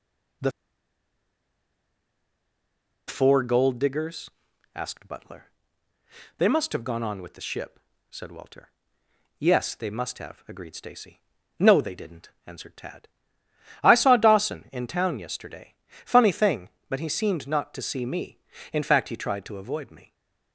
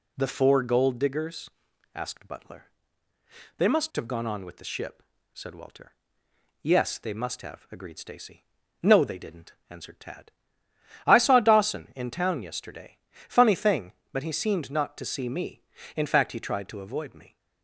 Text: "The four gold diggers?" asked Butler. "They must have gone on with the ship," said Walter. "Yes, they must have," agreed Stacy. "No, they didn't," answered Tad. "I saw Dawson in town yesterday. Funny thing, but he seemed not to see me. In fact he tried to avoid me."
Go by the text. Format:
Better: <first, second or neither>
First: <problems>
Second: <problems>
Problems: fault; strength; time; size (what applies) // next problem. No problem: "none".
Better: second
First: pauses between "The" and "four"; strong; at 0.5 s; 2.5 s long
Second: none